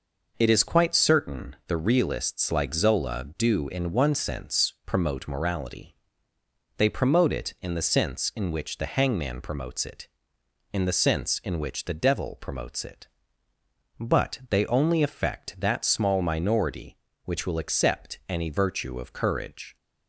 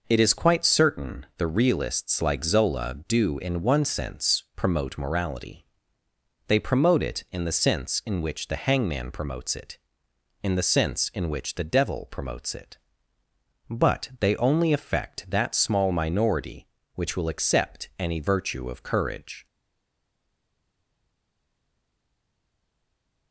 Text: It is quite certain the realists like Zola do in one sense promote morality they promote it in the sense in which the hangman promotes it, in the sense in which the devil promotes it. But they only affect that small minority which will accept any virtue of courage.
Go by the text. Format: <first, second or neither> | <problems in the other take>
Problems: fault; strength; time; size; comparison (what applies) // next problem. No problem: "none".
first | pauses between "morality" and "they"; noticeable; at 5.6 s; 0.84 s long; noticeable in the first // stays silent after the last word; strong; from 19.4 s on; 3.9 s long